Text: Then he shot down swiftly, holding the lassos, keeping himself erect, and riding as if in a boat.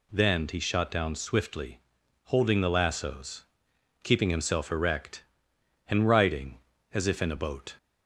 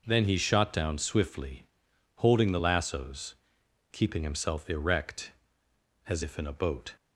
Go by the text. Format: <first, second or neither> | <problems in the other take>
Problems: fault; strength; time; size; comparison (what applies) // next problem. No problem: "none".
first | skips "and riding"; at 5.6 s